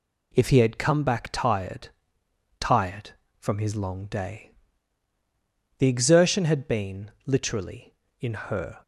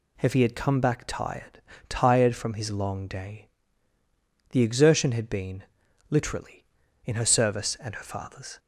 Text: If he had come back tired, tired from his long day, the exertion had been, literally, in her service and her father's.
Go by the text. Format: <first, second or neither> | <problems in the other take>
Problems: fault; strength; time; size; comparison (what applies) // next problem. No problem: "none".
second | stops before "service and her father's"; at 8.8 s